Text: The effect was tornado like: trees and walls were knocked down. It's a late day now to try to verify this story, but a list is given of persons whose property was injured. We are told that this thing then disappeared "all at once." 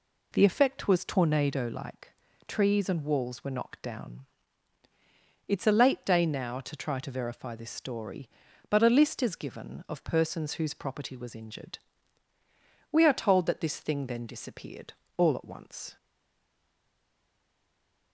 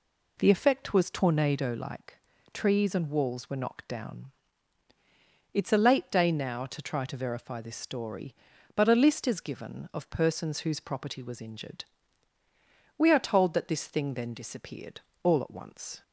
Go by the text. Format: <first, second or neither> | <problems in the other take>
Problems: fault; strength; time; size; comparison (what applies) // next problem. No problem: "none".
second | pauses between "disappeared" and "all"; slight; at 14.9 s; 0.24 s long; slight in the second // stays silent after the last word; from 15.9 s on; 2.2 s long